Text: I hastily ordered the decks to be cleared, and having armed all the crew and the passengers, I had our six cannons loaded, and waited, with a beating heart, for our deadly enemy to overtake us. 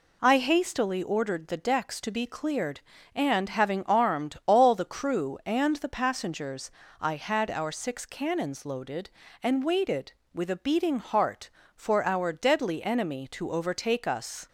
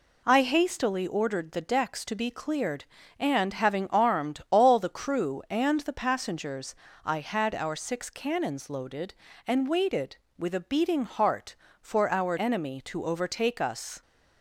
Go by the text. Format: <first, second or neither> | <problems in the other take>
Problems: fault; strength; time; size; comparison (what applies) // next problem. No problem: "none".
first | skips "deadly"; at 12.3 s